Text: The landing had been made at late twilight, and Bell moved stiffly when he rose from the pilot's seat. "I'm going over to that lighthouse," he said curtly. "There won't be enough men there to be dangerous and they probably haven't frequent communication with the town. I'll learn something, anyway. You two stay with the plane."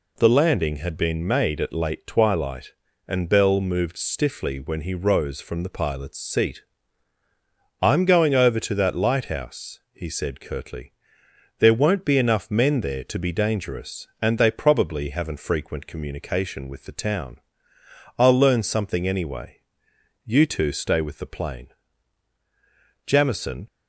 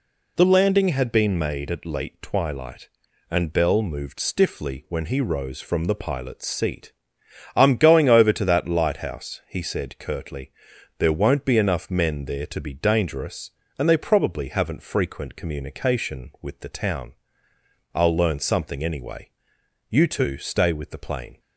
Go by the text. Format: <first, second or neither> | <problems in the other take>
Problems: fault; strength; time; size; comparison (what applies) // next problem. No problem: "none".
second | goes on to say "Jamison"; noticeable; from 23.0 s on; 0.62 s long